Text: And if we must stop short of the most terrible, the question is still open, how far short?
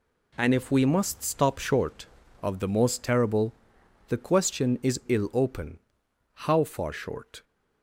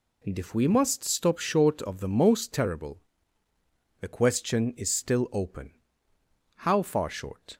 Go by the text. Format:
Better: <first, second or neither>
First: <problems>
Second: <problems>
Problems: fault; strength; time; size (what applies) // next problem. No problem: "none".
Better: second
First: says "ill" for "still"; at 5.0 s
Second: none